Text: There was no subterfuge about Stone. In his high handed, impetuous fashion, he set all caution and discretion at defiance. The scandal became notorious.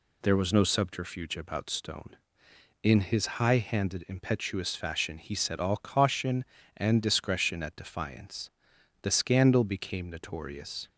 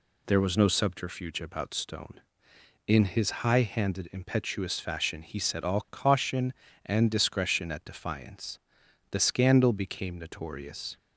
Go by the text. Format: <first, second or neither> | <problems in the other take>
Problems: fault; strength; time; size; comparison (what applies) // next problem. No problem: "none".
neither | none